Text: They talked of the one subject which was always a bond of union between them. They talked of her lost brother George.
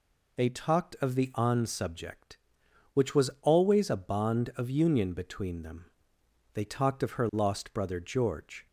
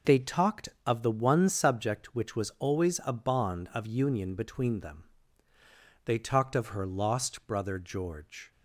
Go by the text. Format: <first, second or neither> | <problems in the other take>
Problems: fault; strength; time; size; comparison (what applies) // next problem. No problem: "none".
second | says "on" for "one"; at 1.3 s